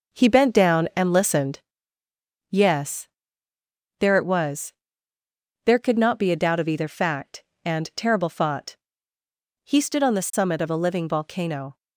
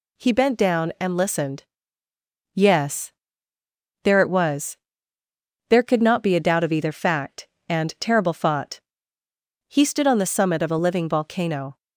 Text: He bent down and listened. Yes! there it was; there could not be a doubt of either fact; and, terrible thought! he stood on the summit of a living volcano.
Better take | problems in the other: second | starts louder than the rest; noticeable; until 1.9 s; 5.5 dB

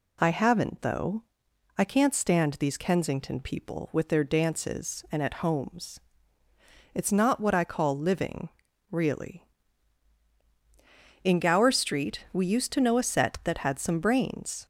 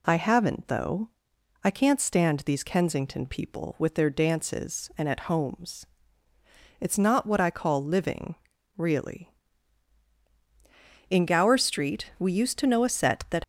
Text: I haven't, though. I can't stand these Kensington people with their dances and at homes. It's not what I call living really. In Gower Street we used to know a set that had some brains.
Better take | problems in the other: first | pauses between "living" and "really"; at 8.3 s; 0.42 s long; also in the first // stops before "had some brains"; at 13.4 s

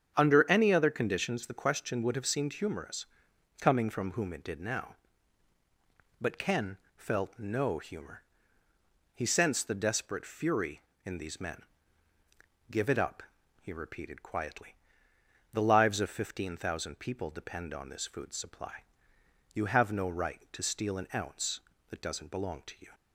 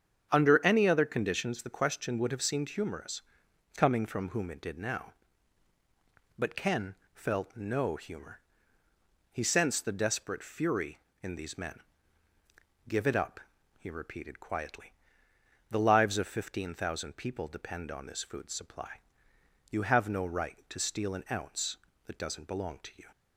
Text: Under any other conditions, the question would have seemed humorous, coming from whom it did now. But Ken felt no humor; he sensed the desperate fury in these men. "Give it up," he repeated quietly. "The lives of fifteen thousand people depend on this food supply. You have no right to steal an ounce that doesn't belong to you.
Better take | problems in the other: neither | starts louder than the rest; strong; the same in both // pauses between "Ken" and "felt"; slight; the same in both

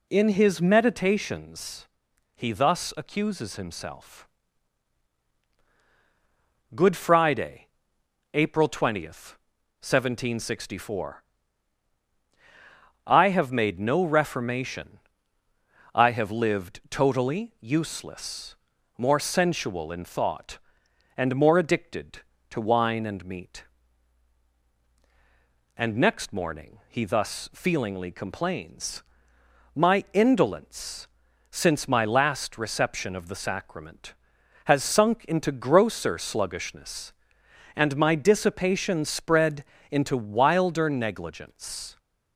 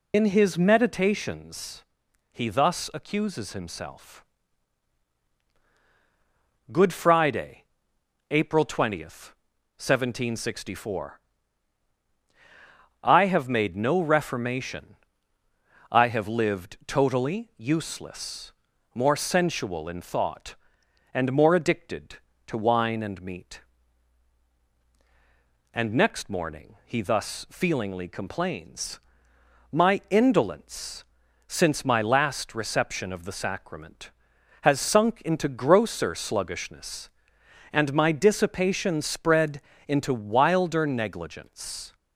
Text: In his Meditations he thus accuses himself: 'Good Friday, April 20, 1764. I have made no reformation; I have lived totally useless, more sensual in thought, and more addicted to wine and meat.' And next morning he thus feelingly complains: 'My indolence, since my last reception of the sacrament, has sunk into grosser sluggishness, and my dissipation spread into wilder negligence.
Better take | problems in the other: first | loses the start of "In"; at 0.1 s; 75 ms // pauses between "Meditations" and "he"; noticeable; at 1.8 s; 0.48 s long; noticeable in the first // pauses between "spread" and "into"; slight; at 39.6 s; 0.28 s long; slight in the first

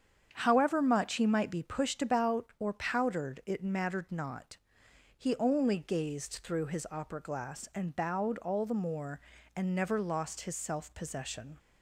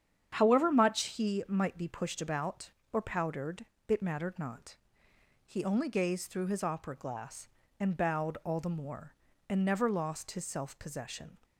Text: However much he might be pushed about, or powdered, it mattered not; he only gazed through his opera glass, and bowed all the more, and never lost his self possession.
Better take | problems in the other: neither | starts louder than the rest; strong; the same in both

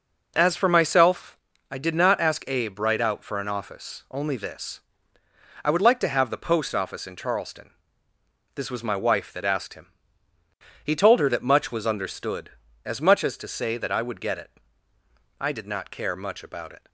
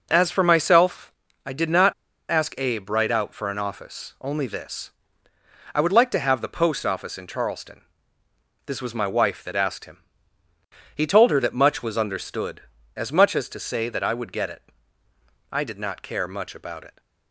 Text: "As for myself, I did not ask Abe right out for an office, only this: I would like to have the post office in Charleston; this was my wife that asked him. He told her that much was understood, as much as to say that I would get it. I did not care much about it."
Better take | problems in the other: first | pauses between "not" and "ask"; at 1.9 s; 0.38 s long

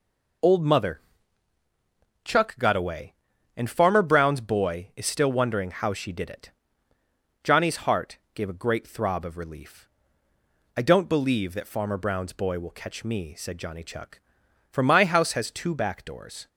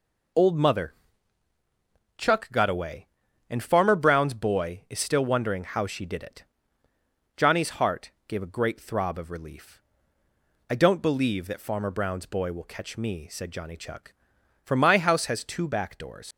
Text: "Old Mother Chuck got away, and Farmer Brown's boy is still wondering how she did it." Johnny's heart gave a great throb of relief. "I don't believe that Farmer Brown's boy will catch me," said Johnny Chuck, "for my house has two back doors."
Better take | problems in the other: first | pauses between "Mother" and "Chuck"; at 0.9 s; 1.2 s long; also in the first // pauses between "heart" and "gave"; slight; at 8.1 s; 0.16 s long; slight in the first // leaves "doors" unfinished; at 16.3 s; 100 ms

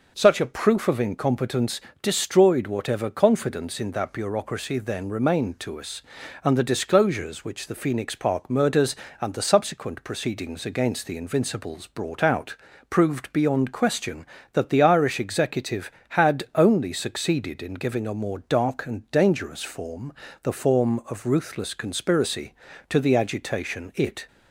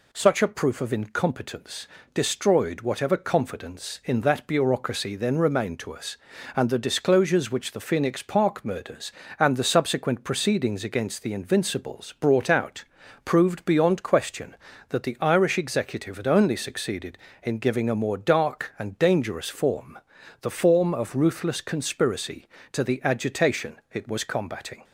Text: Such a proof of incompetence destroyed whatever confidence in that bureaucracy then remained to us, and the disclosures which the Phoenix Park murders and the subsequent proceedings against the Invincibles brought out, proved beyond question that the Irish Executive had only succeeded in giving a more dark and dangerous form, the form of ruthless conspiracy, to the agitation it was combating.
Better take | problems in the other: second | pauses between "incompetence" and "destroyed"; slight; at 1.8 s; 0.20 s long; slight in the second // stops before "was combating"; at 24.2 s

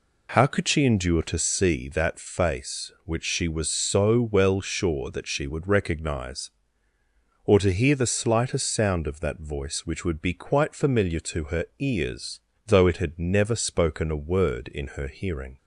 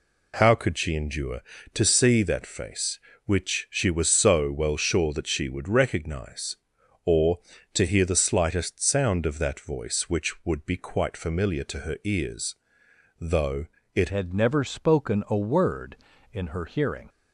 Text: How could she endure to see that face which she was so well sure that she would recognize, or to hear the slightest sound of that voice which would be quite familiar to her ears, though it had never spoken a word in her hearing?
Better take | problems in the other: first | pauses between "though" and "it"; slight; at 13.6 s; 0.28 s long // changes voice at "had"; from 14.1 s on; 2.9 s long

